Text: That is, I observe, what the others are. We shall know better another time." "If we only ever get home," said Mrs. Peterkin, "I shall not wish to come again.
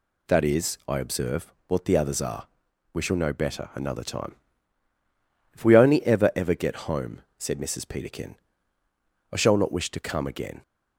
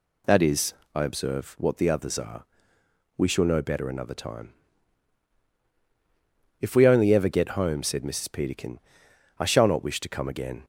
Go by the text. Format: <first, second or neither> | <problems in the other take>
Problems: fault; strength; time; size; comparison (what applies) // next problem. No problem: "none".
second | says "ever" twice; at 6.3 s